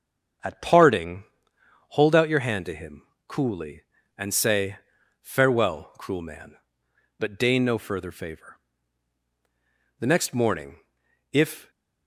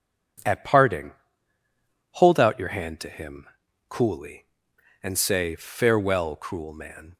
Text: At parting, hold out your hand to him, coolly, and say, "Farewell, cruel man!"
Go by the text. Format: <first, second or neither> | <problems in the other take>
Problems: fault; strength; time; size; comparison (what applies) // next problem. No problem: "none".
second | starts louder than the rest; until 2.0 s; 6.5 dB // goes on to say "but deign no further favor The next morning if"; strong; from 7.1 s on; 4.5 s long